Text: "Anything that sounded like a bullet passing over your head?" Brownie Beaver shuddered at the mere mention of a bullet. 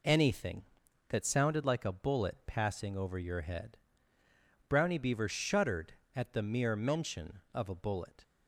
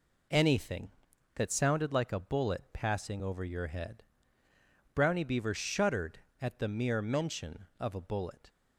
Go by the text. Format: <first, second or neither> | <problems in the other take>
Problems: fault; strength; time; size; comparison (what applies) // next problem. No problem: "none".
neither | none